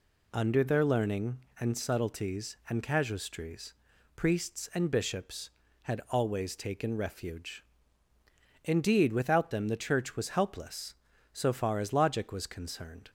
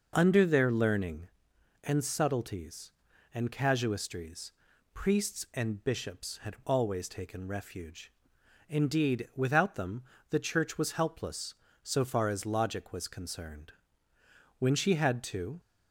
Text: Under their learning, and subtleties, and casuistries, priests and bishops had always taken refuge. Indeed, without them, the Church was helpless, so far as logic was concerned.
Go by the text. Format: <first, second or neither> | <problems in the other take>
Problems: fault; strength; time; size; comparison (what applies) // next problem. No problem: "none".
first | goes on to say "When she had to"; noticeable; from 14.5 s on; 1.0 s long